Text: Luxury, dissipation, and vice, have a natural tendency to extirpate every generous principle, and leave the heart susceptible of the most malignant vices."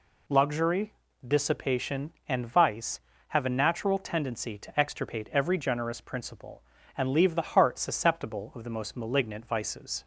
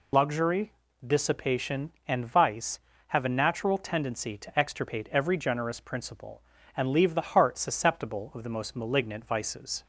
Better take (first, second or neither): first